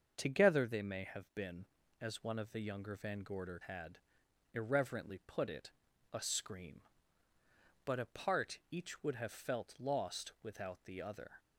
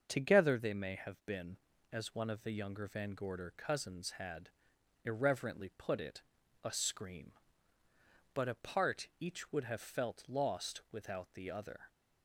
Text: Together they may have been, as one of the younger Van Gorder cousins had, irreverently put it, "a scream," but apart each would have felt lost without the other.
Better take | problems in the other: second | starts louder than the rest; until 1.1 s; 6.5 dB; also in the second // skips "cousins"; at 3.6 s

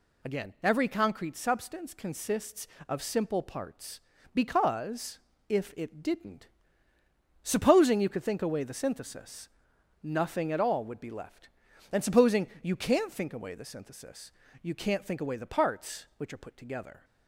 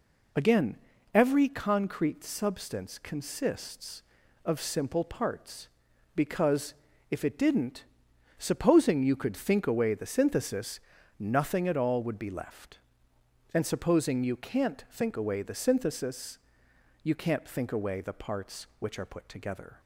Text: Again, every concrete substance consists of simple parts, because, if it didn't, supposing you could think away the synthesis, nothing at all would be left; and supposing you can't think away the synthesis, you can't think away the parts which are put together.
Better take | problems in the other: neither | none

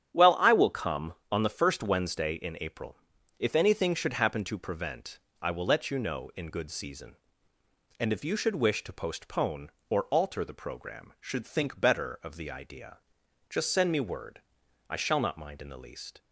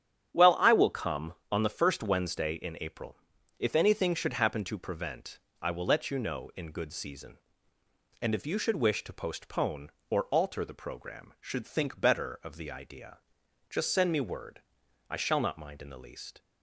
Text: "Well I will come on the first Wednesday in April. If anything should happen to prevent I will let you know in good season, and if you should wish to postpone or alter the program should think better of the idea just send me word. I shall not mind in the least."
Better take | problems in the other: neither | starts louder than the rest; strong; the same in both // pauses between "prevent" and "I"; slight; the same in both // pauses between "idea" and "just"; noticeable; the same in both

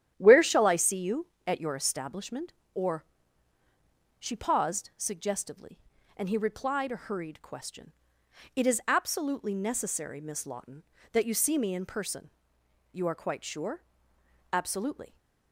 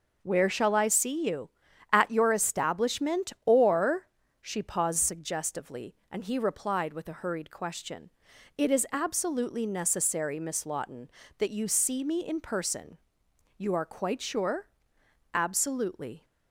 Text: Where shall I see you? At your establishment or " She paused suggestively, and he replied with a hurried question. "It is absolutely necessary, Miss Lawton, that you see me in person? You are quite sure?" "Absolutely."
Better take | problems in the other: second | starts louder than the rest; strong; until 1.1 s; 9.5 dB // skips "with"; at 6.9 s

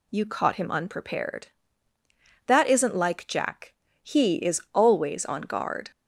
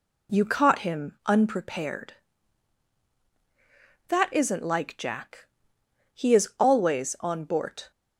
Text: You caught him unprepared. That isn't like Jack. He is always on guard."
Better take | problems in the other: first | says "bort" for "guard"; at 7.4 s

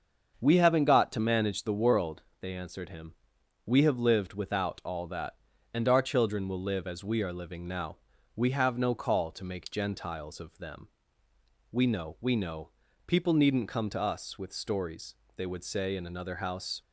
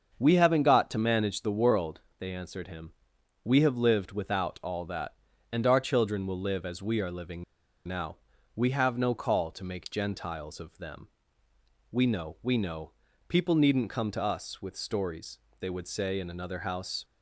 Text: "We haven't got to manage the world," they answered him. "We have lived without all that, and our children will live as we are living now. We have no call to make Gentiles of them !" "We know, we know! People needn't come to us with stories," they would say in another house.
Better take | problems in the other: first | starts louder than the rest; until 1.2 s; 7 dB; also in the first // pauses between "living" and "now"; at 7.4 s; 0.44 s long

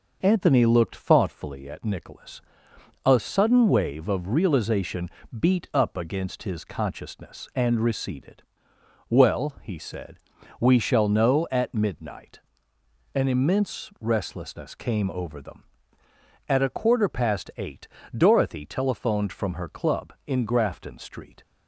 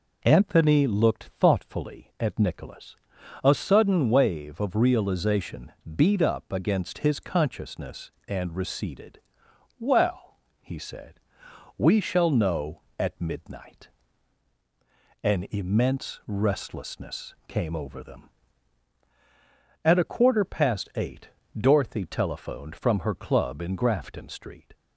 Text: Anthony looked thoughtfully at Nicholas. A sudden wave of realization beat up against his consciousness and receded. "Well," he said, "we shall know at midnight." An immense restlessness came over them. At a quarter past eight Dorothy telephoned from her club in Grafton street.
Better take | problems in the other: neither | pauses between "realization" and "beat"; slight; the same in both // pauses between "eight" and "Dorothy"; slight; the same in both

